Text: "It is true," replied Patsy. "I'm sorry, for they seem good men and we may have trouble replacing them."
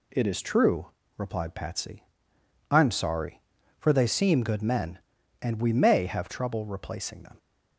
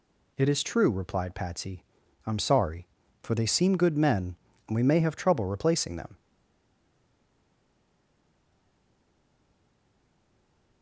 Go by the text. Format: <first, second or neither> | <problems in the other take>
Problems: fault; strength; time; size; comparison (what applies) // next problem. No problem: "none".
first | stays silent after the last word; strong; from 6.1 s on; 4.7 s long